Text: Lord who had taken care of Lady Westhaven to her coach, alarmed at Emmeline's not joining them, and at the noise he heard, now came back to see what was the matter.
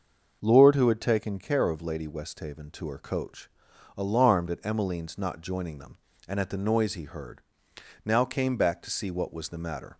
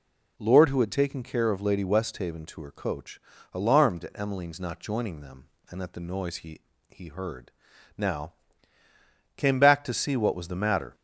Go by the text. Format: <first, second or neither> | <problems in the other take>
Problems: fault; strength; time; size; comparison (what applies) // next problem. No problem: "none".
first | says "he" twice; at 6.9 s // pauses between "now" and "came"; at 8.3 s; 1.0 s long